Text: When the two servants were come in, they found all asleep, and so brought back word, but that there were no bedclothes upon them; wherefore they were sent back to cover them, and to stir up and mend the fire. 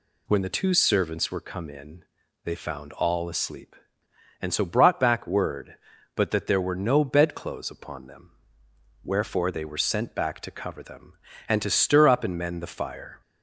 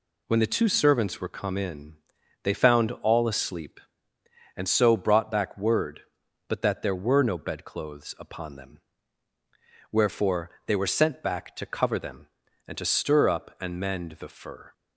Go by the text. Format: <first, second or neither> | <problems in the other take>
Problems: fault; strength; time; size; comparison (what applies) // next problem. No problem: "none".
first | pauses between "wherefore" and "they"; slight; at 10.4 s; 0.18 s long // says "fur" for "fire"; at 14.2 s